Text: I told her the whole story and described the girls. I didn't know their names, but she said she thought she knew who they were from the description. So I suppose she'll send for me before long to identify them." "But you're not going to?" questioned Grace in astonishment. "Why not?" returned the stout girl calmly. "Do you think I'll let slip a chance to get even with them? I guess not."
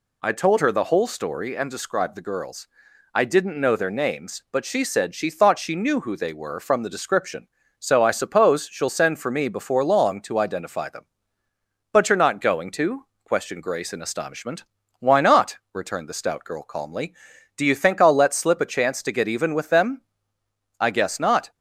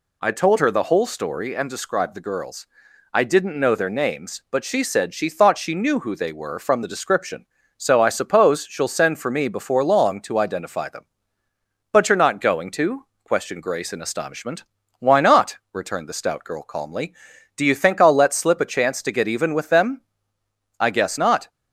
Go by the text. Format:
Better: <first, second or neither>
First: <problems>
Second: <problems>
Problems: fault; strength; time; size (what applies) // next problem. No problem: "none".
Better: neither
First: none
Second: none